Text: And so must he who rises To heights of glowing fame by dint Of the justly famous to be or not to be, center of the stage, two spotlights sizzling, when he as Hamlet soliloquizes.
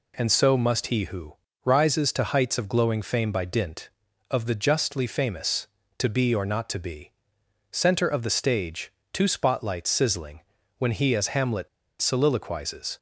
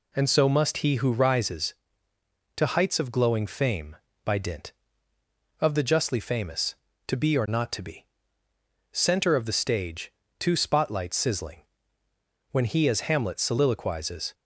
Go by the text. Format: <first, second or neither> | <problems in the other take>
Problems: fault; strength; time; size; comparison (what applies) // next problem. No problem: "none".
second | pauses between "who" and "rises"; slight; at 1.3 s; 0.32 s long // pauses between "Hamlet" and "soliloquizes"; slight; at 11.6 s; 0.33 s long